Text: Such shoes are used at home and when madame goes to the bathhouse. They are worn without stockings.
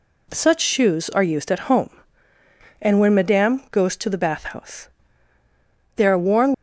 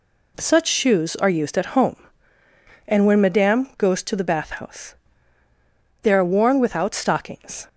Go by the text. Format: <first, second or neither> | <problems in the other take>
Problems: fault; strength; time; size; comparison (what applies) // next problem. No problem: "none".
second | stops before "without stockings"; at 6.5 s